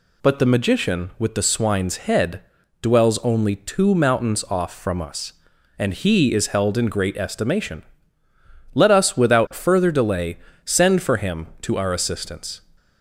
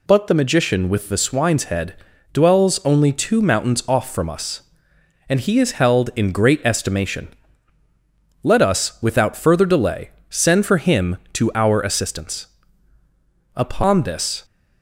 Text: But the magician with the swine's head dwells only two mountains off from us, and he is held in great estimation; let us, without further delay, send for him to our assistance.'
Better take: first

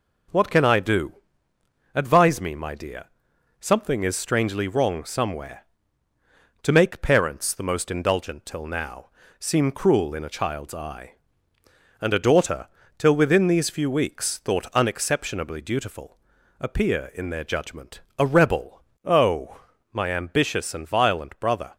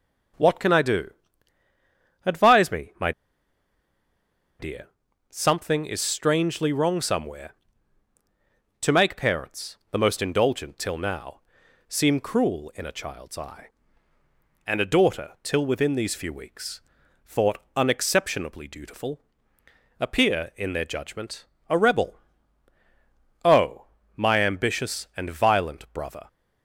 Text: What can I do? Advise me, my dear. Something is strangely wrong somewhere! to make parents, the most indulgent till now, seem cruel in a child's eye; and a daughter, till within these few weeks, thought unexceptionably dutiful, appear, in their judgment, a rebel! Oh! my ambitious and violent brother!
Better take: first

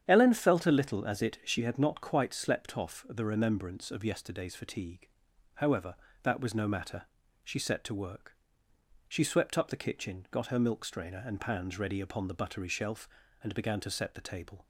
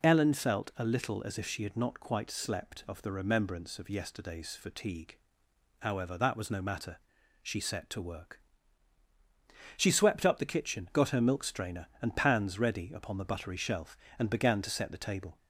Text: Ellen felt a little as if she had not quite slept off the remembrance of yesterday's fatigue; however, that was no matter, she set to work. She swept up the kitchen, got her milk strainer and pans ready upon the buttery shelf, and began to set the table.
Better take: second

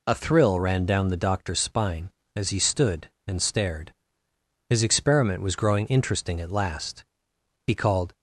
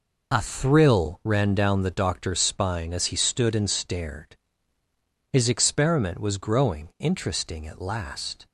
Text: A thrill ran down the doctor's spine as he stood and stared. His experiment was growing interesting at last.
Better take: second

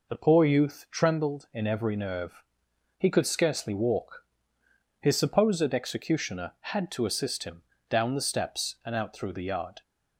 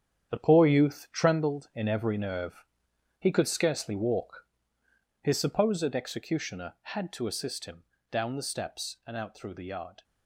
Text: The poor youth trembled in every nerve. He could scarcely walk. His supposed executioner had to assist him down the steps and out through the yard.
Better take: first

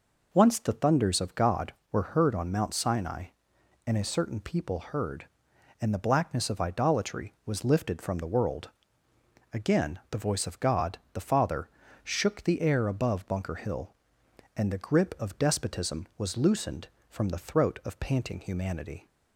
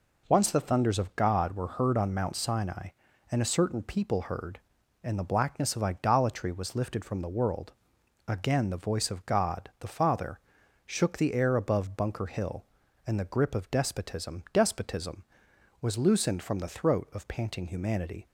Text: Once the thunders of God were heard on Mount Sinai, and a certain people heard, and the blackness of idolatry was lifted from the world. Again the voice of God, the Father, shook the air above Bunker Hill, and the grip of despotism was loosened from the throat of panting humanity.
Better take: first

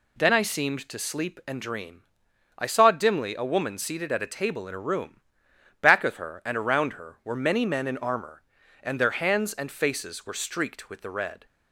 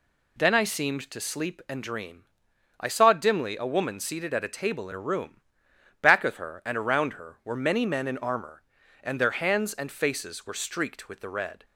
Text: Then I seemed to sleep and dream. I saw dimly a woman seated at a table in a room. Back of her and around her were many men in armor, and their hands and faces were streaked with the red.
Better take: neither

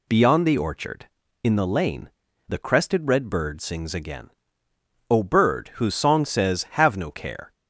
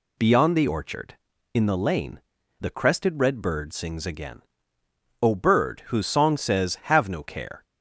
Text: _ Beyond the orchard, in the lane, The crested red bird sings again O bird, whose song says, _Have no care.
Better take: neither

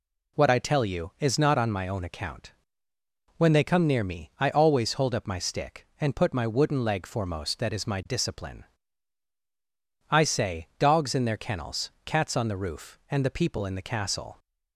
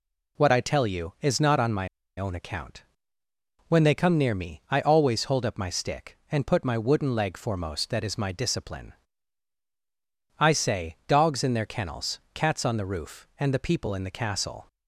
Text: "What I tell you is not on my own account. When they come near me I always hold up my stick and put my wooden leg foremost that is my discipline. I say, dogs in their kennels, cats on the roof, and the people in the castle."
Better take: first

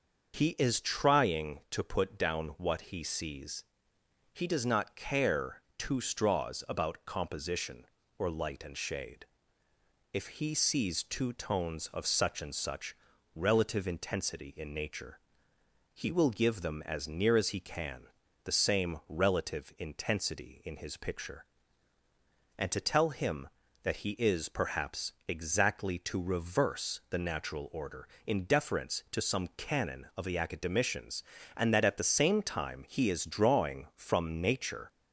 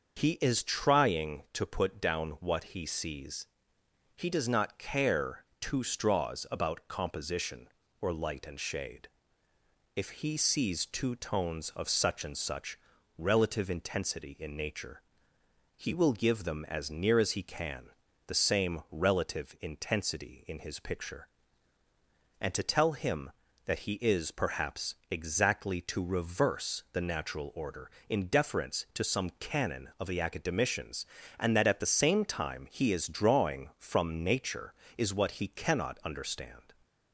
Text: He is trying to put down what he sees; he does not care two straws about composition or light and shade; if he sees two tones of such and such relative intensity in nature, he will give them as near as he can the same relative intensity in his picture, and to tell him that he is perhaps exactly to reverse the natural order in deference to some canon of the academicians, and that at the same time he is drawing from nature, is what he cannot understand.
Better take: second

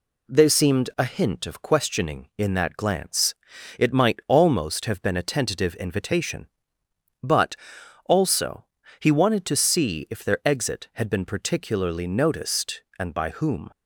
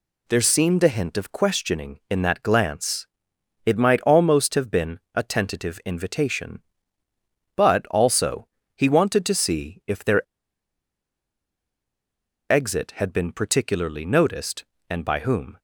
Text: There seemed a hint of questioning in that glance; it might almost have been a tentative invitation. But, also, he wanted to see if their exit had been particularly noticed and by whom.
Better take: first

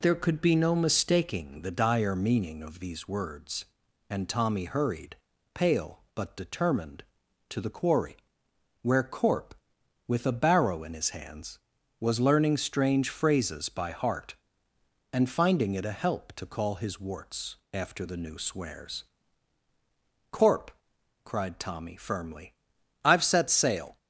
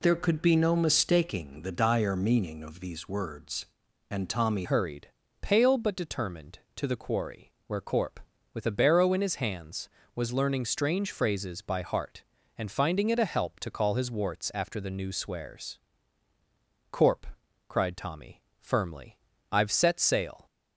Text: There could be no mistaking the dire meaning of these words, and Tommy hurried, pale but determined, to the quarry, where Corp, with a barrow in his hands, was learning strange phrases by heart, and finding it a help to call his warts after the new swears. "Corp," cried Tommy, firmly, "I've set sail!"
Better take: first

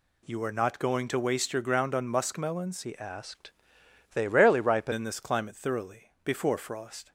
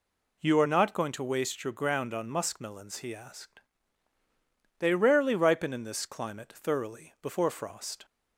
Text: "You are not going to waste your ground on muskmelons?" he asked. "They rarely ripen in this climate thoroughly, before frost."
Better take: second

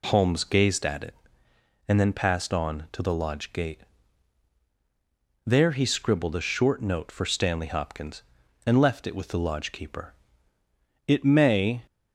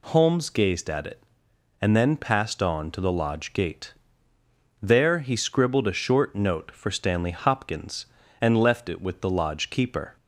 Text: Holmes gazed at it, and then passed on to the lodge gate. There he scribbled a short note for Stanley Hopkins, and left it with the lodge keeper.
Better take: second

